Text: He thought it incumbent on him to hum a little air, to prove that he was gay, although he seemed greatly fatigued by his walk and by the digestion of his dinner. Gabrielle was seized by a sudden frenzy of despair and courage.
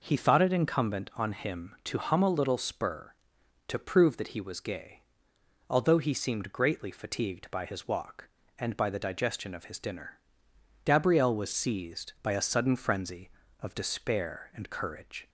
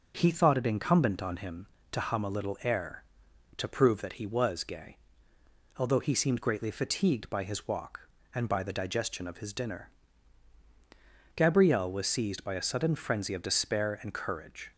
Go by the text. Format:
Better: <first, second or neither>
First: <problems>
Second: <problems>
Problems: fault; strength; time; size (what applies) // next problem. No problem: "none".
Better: second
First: says "spur" for "air"; at 2.5 s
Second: none